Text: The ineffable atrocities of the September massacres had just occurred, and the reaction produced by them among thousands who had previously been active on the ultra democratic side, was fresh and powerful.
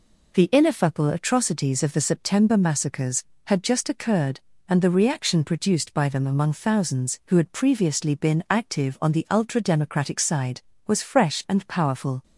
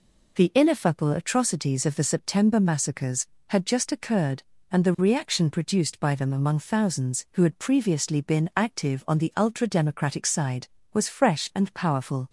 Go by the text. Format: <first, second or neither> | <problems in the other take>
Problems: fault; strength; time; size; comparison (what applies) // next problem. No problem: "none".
neither | none